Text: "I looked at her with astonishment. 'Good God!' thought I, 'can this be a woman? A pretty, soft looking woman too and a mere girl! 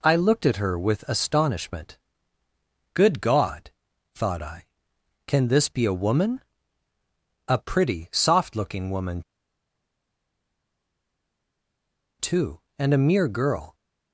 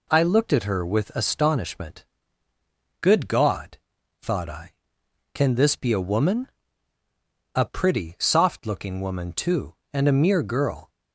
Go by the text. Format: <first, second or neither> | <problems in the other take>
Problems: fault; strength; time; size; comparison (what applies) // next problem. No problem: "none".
second | pauses between "woman" and "too"; strong; at 9.2 s; 2.9 s long